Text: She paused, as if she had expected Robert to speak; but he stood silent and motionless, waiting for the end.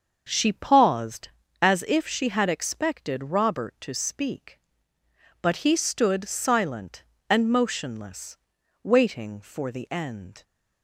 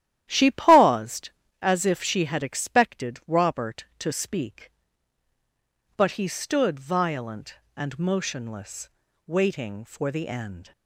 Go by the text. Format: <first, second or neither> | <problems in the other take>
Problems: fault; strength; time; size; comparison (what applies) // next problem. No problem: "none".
first | starts louder than the rest; strong; until 1.3 s; 12 dB; also in the first // says "violent" for "silent"; at 6.7 s